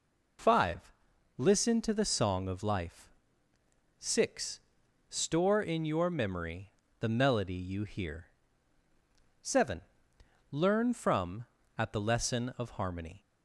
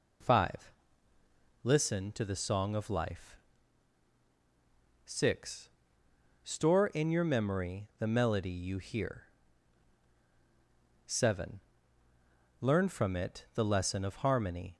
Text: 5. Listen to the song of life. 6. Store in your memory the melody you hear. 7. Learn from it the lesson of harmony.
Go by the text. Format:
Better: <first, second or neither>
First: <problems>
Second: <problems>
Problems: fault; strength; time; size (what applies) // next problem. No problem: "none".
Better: second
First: pauses between "memory" and "the"; slight; at 6.6 s; 0.30 s long // says "at" for "it"; at 11.7 s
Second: none